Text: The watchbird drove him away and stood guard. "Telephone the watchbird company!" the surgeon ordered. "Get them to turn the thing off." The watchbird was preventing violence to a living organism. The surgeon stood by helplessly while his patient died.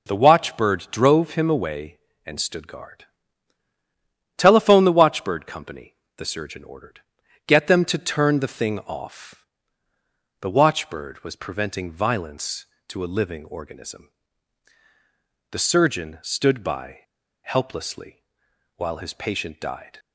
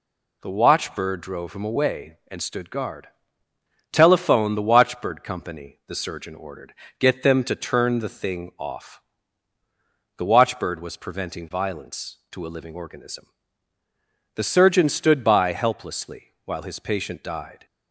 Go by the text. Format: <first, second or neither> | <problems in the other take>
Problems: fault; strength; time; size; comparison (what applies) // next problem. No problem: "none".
second | pauses between "by" and "helplessly"; at 17.0 s; 0.42 s long // pauses between "helplessly" and "while"; noticeable; at 18.2 s; 0.54 s long